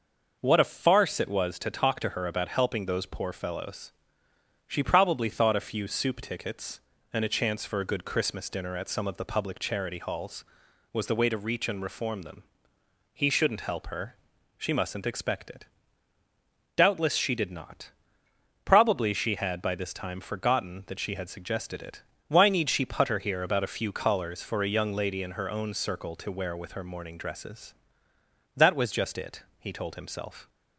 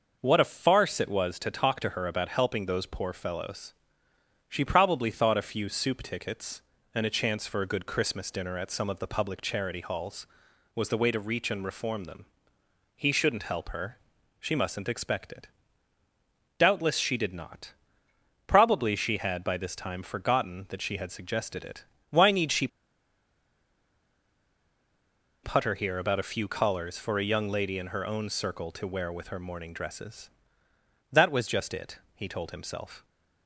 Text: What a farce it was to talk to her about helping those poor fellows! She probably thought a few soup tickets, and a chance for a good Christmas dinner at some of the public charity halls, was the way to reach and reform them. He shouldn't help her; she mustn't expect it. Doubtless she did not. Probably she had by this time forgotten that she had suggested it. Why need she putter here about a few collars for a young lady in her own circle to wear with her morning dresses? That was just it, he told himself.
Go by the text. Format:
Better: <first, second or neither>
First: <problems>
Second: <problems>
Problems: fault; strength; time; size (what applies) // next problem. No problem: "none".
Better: first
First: none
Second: pauses between "she" and "putter"; strong; at 22.6 s; 2.7 s long